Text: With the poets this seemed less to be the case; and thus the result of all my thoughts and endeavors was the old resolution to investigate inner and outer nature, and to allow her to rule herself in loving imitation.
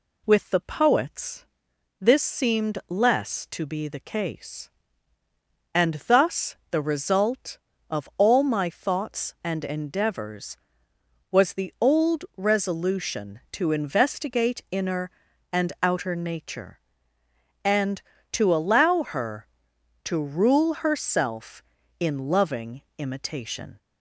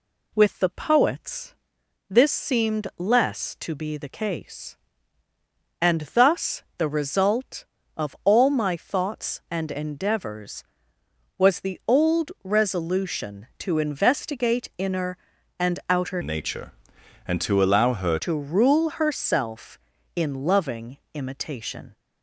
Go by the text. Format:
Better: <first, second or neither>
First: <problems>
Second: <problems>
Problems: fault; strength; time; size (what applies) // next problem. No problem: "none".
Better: first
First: pauses between "poets" and "this"; noticeable; at 1.4 s; 0.56 s long // pauses between "thus" and "the"; slight; at 6.5 s; 0.16 s long // pauses between "loving" and "imitation"; slight; at 22.8 s; 0.16 s long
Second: pauses between "poets" and "this"; noticeable; at 1.5 s; 0.56 s long // pauses between "thus" and "the"; slight; at 6.6 s; 0.16 s long // changes voice from "nature" to "her"; from 16.2 to 18.1 s; 1.9 s long // pauses between "loving" and "imitation"; slight; at 20.9 s; 0.16 s long